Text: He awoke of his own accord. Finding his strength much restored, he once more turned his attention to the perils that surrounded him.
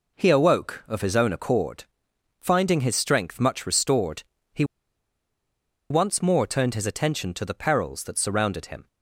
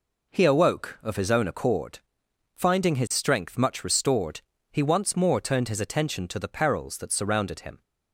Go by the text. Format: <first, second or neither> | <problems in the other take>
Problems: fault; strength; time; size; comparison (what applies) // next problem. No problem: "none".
second | pauses between "he" and "once"; strong; at 4.6 s; 1.2 s long